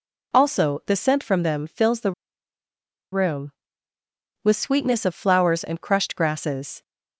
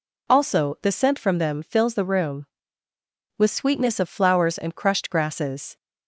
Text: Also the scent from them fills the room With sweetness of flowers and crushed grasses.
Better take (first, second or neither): second